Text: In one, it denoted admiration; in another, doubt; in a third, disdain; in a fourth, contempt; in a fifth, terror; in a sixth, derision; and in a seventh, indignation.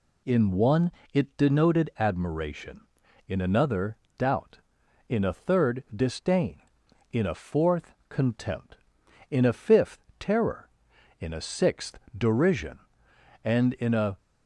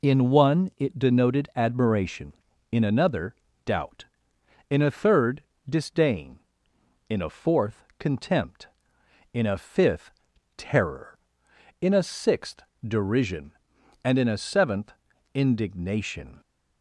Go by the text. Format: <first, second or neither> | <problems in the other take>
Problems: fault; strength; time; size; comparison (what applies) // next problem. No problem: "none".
second | stops before "seventh indignation"; at 14.1 s